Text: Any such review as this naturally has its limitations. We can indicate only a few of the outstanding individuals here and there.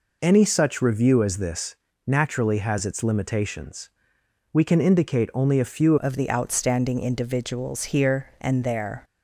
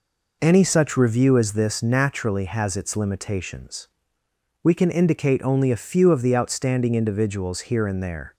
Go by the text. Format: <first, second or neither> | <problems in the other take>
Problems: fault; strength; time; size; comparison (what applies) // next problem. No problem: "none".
second | pauses between "this" and "naturally"; slight; at 1.7 s; 0.32 s long // changes voice at "of"; from 6.0 s on; 3.0 s long